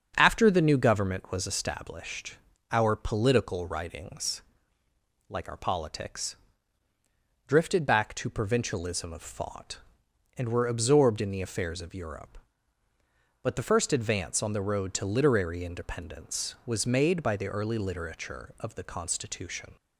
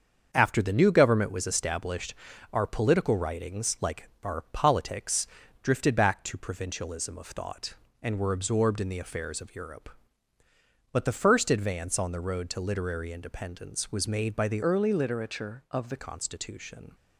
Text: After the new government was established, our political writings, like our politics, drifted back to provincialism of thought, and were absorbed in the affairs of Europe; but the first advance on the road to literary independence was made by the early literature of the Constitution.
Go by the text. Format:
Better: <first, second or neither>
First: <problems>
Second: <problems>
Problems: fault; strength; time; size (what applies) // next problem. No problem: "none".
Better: first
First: starts louder than the rest; until 1.1 s; 7 dB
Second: starts louder than the rest; until 1.3 s; 7 dB // changes voice from "early" to "the"; from 14.6 to 15.9 s; 1.3 s long